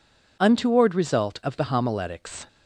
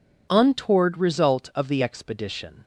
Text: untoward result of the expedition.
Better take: second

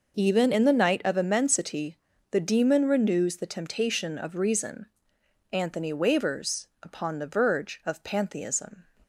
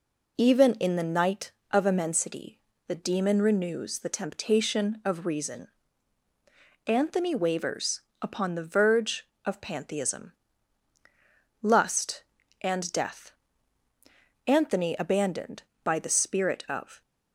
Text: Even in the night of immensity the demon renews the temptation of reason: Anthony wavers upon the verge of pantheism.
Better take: first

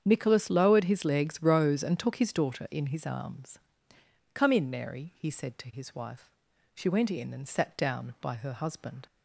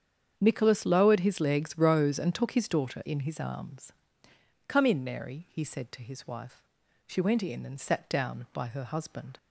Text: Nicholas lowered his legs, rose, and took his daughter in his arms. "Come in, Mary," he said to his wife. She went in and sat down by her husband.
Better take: neither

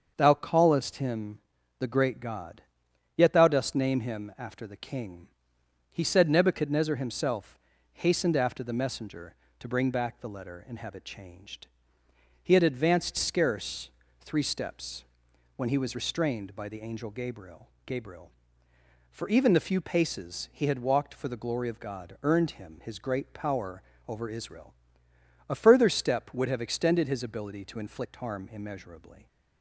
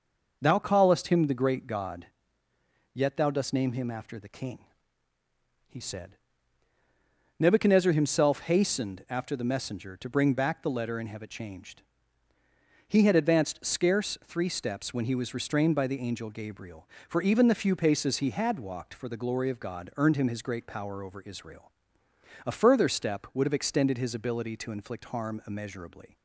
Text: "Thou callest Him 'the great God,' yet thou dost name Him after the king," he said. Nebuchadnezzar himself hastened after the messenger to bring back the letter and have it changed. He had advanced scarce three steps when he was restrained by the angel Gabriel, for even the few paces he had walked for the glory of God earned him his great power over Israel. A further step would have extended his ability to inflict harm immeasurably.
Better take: second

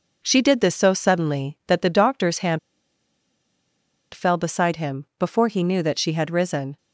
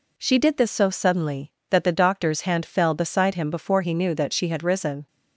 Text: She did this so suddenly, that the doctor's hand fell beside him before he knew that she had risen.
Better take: second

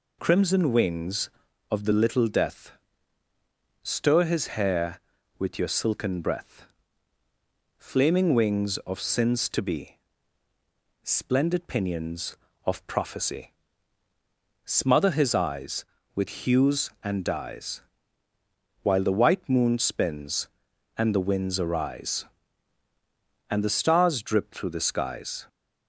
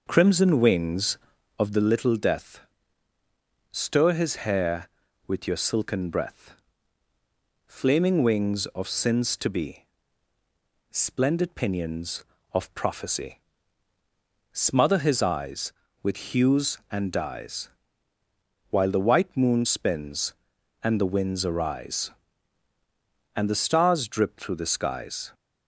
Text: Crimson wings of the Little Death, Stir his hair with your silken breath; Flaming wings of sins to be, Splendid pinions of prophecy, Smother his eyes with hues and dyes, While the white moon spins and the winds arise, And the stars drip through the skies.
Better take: first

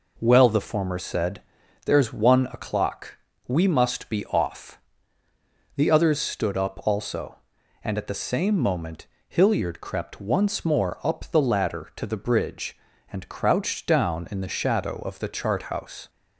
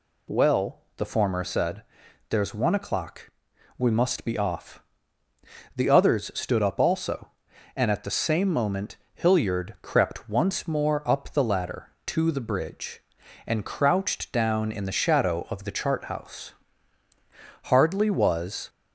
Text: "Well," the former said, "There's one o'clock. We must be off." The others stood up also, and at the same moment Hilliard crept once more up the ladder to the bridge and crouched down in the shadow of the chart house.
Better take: first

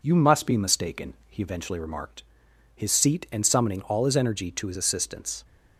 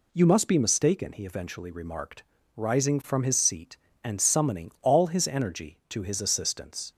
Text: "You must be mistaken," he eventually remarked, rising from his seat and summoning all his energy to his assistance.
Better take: second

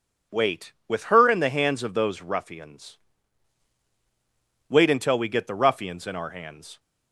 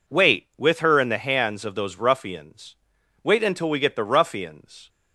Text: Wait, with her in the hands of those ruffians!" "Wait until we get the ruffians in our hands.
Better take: first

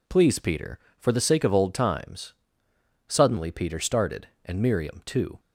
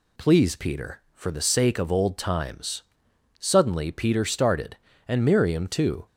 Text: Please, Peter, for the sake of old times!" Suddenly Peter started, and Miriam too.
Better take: neither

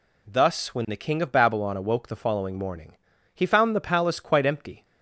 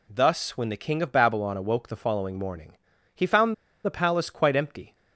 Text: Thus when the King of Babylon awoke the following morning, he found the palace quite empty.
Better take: first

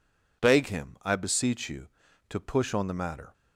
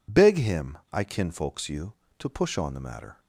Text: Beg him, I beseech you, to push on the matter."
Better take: first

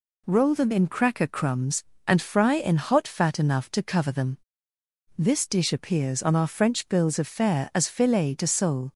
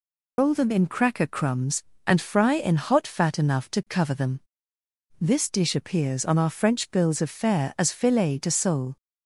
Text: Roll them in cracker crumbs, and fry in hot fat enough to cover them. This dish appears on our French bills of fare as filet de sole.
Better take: first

